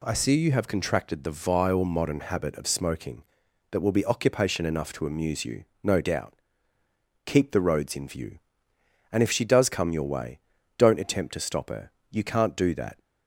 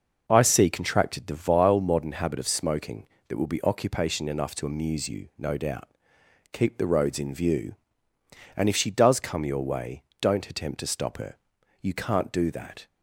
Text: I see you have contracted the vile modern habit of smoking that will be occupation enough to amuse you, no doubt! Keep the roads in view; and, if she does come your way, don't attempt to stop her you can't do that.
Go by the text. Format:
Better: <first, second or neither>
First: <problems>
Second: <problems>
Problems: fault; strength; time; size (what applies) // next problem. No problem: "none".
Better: first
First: pauses between "her" and "you"; slight; at 11.9 s; 0.20 s long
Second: skips "you have"; at 0.6 s // pauses between "her" and "you"; at 11.3 s; 0.44 s long